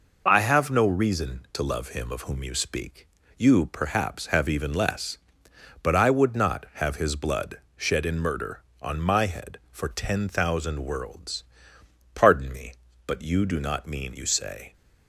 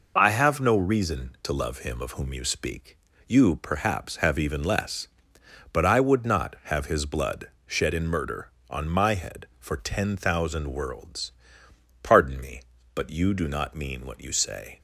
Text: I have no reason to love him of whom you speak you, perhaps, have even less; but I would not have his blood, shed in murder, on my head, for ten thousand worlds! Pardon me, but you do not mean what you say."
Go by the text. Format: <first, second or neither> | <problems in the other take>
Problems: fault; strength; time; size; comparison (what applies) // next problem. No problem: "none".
second | pauses between "speak" and "you"; slight; at 3.0 s; 0.32 s long; slight in the second // skips "what"; at 14.1 s